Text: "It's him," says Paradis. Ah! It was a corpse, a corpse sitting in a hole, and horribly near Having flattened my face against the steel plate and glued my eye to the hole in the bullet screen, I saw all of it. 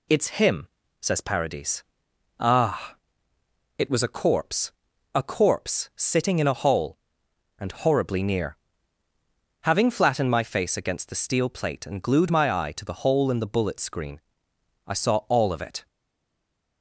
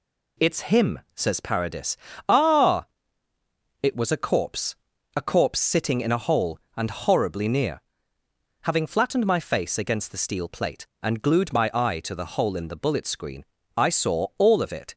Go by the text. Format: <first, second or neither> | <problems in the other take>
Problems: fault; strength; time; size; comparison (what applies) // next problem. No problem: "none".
second | pauses between "near" and "Having"; at 8.5 s; 1.0 s long; noticeable in the second // stays silent after the last word; from 15.8 s on; 1.0 s long